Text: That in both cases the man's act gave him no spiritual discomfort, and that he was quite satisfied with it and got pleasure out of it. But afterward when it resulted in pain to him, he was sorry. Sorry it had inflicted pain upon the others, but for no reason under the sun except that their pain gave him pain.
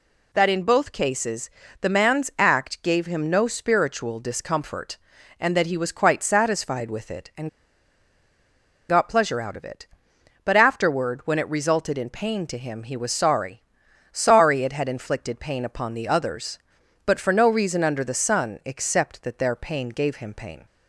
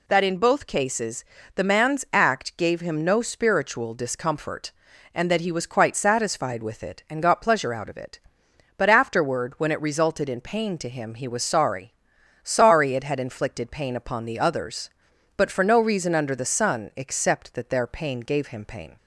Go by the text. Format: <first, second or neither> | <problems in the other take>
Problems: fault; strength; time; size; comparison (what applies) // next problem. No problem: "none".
second | pauses between "cases" and "the"; slight; at 1.4 s; 0.32 s long; slight in the second // pauses between "and" and "got"; strong; at 7.4 s; 1.4 s long